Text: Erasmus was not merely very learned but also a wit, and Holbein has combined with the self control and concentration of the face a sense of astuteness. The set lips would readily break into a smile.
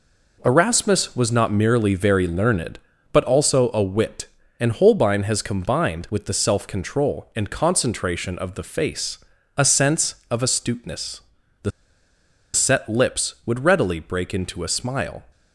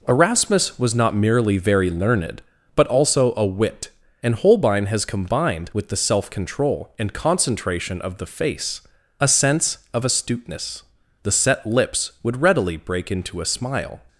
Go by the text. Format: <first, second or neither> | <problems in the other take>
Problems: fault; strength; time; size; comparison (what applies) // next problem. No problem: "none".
second | pauses between "face" and "a"; at 9.1 s; 0.40 s long; also in the second // pauses between "The" and "set"; noticeable; at 11.7 s; 0.83 s long